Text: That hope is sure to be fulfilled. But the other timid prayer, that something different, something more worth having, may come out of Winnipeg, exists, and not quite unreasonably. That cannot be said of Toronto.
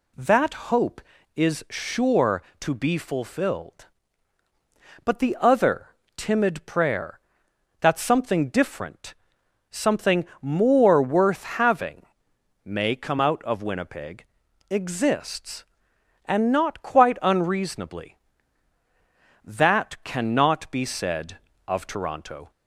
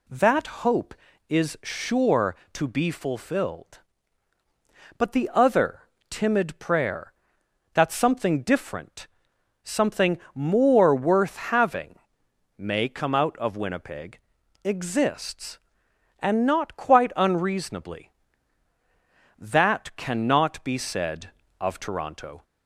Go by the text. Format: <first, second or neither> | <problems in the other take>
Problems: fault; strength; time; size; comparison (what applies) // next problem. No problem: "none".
neither | pauses between "That" and "hope"; slight; the same in both // pauses between "other" and "timid"; slight; the same in both // pauses between "something" and "more"; slight; the same in both